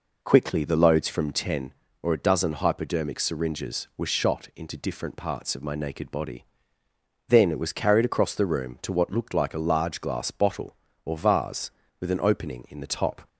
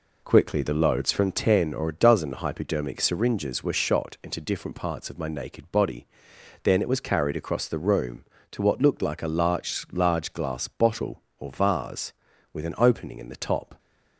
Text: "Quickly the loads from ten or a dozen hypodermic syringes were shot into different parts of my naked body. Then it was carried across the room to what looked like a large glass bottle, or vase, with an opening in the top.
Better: first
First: none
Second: says "large" twice; at 9.9 s

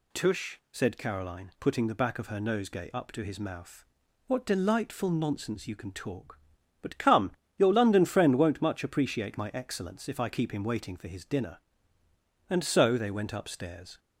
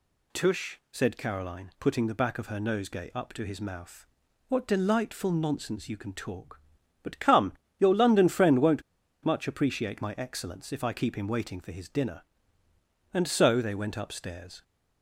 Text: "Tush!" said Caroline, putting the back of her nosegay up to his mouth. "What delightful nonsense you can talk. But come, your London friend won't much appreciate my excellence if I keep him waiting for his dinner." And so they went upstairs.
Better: first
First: none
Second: pauses between "won't" and "much"; at 8.8 s; 0.42 s long

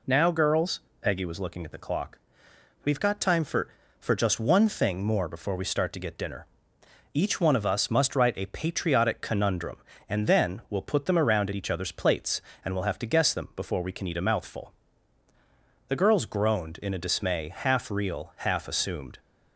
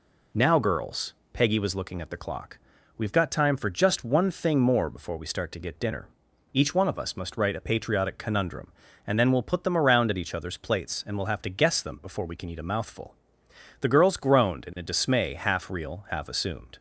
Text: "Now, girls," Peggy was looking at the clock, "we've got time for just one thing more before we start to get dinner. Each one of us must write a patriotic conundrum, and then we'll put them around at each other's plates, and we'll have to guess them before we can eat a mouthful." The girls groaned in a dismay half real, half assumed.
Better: second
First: says "for" twice; at 4.0 s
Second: none

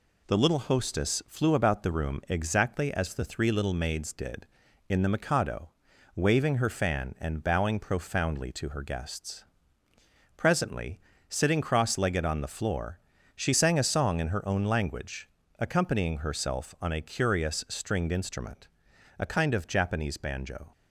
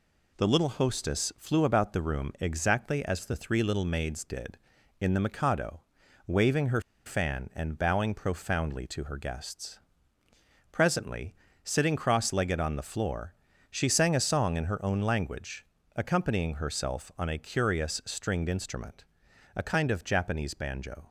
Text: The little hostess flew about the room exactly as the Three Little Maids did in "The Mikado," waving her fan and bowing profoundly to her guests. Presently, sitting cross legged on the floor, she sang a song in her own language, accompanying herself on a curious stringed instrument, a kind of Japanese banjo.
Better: first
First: none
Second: pauses between "her" and "fan"; slight; at 6.8 s; 0.25 s long

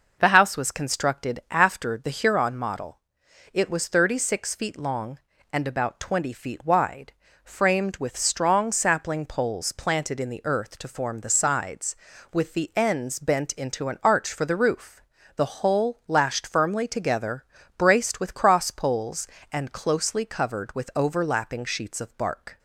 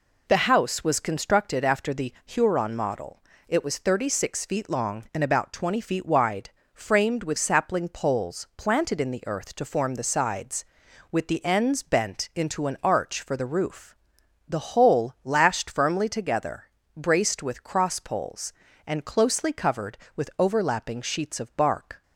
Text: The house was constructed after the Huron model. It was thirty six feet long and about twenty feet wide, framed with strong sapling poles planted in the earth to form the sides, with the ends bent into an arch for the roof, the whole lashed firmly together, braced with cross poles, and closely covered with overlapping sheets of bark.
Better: first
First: none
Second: skips "strong"; at 7.3 s

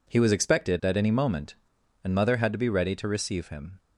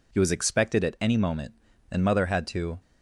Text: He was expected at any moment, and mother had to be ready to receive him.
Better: first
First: none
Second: stops before "be ready to receive him"; at 2.8 s

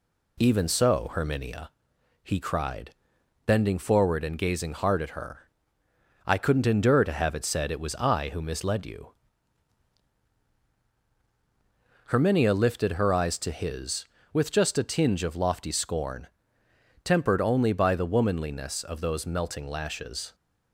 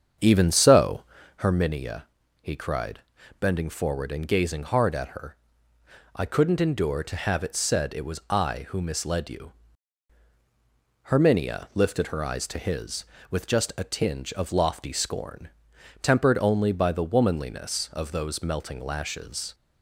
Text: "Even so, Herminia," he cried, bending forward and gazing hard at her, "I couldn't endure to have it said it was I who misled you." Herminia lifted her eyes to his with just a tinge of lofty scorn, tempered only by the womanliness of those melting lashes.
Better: first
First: none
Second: starts louder than the rest; strong; until 1.5 s; 7.5 dB

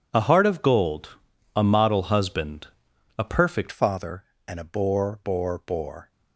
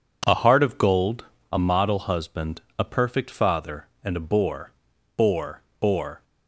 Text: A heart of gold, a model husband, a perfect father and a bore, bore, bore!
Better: second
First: changes voice at "father"; from 3.7 s on; 2.4 s long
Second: none

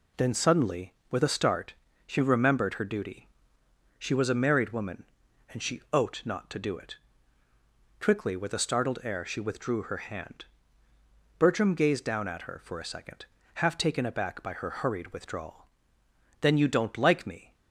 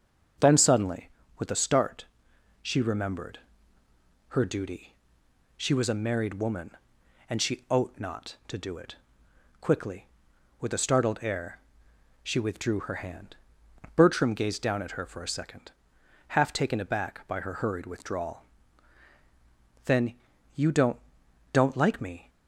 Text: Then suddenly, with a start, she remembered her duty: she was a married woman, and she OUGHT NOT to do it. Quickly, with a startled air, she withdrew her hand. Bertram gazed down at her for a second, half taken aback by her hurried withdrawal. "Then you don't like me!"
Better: first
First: none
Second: starts louder than the rest; strong; until 1.6 s; 7.5 dB // pauses between "remembered" and "her"; noticeable; at 3.3 s; 0.90 s long // pauses between "Then" and "you"; at 20.1 s; 0.42 s long // says "don't" twice; at 21.5 s

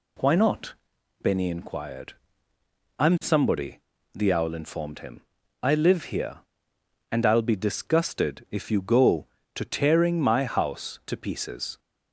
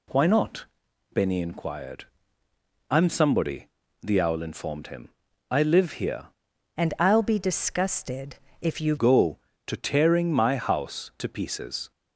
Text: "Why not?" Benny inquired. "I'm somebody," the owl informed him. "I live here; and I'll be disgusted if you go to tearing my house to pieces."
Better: first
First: none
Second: changes voice from "and" to "you"; from 6.7 to 8.9 s; 2.2 s long // pauses between "disgusted" and "if"; slight; at 8.3 s; 0.26 s long

